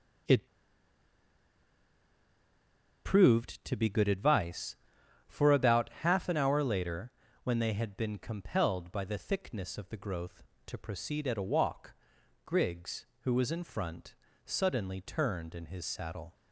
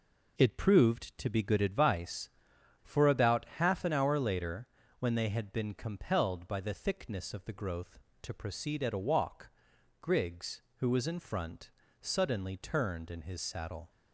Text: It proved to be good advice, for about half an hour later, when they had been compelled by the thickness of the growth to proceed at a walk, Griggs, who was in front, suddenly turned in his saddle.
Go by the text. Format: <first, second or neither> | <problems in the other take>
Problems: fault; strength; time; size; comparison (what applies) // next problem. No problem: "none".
second | pauses between "It" and "proved"; strong; at 0.4 s; 2.5 s long